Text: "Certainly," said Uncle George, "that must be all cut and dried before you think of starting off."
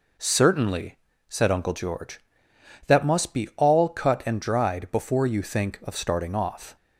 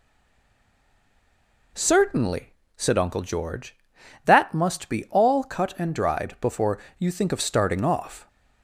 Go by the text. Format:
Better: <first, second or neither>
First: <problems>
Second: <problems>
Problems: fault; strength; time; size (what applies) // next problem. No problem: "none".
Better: first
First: none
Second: stays silent before the first word; noticeable; until 1.7 s; 1.7 s long // pauses between "before" and "you"; slight; at 6.7 s; 0.22 s long